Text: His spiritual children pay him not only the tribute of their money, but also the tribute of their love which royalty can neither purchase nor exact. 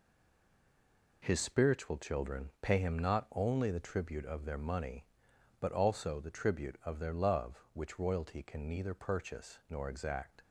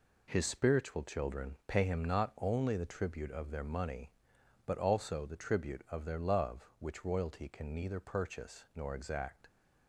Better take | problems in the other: second | stays silent before the first word; noticeable; until 1.2 s; 1.2 s long

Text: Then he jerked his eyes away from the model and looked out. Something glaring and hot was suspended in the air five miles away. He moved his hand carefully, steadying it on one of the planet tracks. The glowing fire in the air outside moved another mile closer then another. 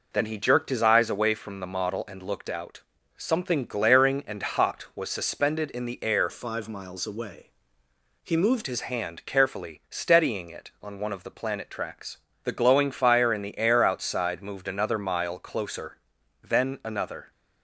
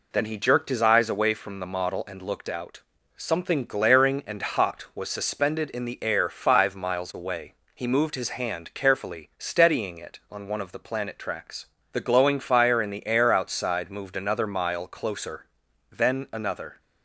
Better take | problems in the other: second | changes voice from "five" to "moved"; from 6.2 to 8.6 s; 2.4 s long // pauses between "closer" and "then"; noticeable; at 15.9 s; 0.50 s long; noticeable in the second

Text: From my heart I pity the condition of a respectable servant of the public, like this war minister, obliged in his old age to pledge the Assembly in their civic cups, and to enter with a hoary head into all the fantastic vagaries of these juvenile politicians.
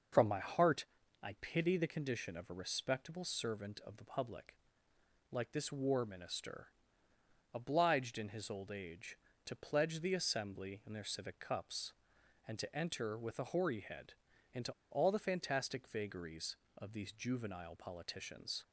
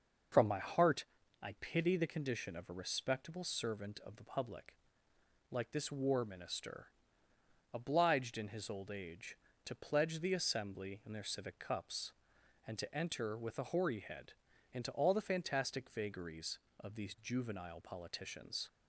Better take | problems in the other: second | starts louder than the rest; until 1.6 s; 6 dB; noticeable in the second // pauses between "heart" and "I"; at 0.8 s; 0.38 s long; also in the second // pauses between "head" and "into"; at 14.1 s; 0.38 s long; also in the second // pauses between "into" and "all"; slight; at 14.7 s; 0.19 s long

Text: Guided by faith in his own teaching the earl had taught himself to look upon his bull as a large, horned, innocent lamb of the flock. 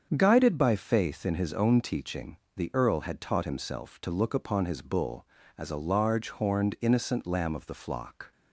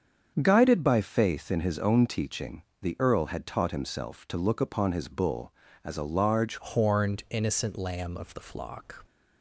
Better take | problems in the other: first | starts louder than the rest; strong; until 1.4 s; 7.5 dB; strong in the first // pauses between "teaching" and "the"; slight; at 2.6 s; 0.18 s long; slight in the first // changes voice at "horned"; from 6.5 s on; 2.5 s long

